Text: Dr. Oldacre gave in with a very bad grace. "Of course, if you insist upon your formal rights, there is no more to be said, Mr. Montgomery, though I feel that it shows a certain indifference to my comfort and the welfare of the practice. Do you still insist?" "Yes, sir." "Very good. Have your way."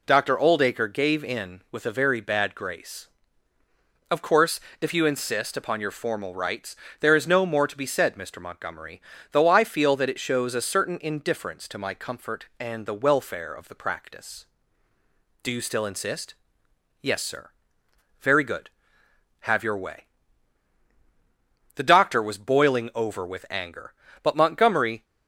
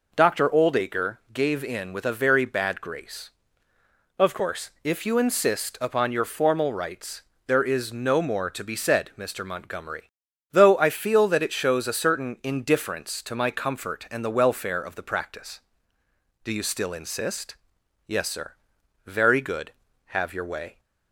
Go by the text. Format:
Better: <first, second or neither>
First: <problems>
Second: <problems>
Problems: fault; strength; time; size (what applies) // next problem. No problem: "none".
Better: second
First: goes on to say "The doctor was boiling over with anger but Montgomery"; strong; from 21.7 s on; 3.2 s long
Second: none